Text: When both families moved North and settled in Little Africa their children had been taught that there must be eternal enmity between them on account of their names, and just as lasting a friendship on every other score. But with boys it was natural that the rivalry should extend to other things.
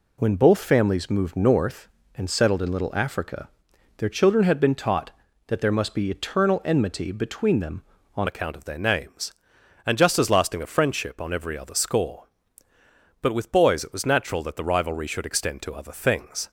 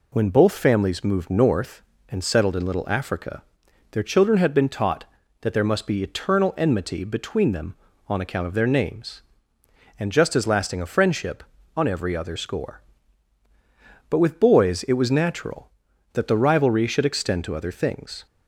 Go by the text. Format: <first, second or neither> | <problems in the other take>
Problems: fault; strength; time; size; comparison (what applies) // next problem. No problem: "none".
second | pauses between "Africa" and "their"; noticeable; at 3.4 s; 0.50 s long; noticeable in the second // changes voice at "account"; from 8.2 s on; 8.2 s long